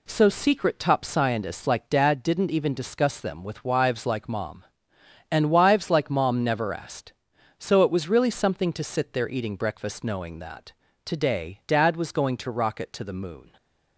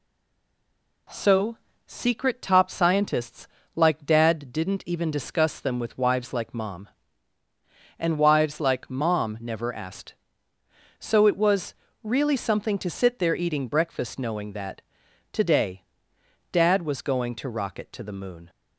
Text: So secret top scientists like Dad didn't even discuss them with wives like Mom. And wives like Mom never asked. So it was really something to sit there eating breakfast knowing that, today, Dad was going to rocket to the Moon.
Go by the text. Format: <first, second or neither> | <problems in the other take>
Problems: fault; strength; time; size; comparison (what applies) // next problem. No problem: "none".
first | stays silent before the first word; until 1.0 s; 1.0 s long // pauses between "So" and "secret"; slight; at 1.5 s; 0.30 s long // pauses between "scientists" and "like"; slight; at 3.4 s; 0.28 s long // pauses between "was" and "really"; slight; at 11.7 s; 0.28 s long